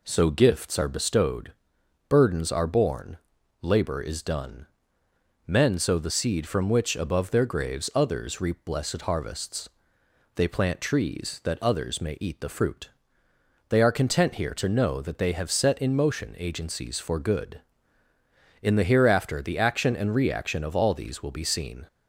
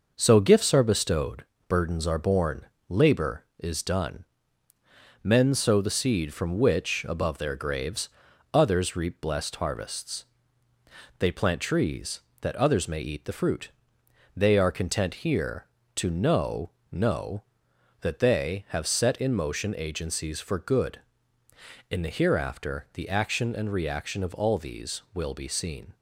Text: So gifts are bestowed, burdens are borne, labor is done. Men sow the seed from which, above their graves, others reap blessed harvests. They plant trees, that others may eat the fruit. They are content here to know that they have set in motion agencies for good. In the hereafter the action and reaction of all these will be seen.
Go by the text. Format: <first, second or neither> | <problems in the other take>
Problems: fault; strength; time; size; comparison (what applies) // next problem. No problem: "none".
first | says "know" twice; at 16.9 s